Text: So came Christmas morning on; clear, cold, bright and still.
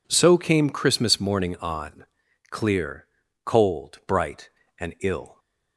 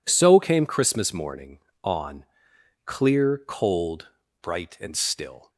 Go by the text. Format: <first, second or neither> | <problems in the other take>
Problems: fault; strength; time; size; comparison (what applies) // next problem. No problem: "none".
second | says "ill" for "still"; at 5.0 s